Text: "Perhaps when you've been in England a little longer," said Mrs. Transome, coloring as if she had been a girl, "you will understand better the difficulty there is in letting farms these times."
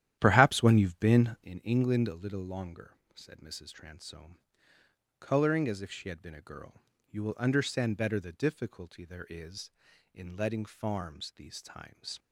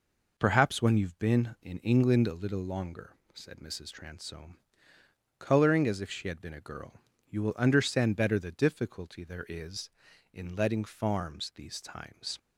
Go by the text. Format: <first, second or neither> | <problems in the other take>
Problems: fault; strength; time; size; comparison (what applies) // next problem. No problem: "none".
second | starts louder than the rest; strong; until 1.5 s; 11.5 dB